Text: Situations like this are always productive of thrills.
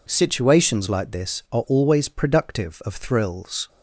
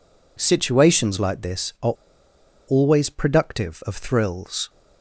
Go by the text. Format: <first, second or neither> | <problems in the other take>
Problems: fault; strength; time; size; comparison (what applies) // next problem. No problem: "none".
first | pauses between "are" and "always"; noticeable; at 1.9 s; 0.73 s long